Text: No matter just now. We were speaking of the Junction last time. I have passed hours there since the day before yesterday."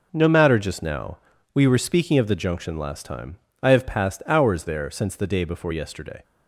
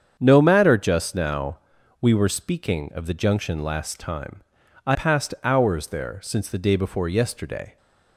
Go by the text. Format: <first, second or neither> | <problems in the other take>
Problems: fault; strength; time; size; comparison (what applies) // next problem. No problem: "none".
first | starts louder than the rest; strong; until 1.2 s; 7.5 dB // skips "have"; at 4.9 s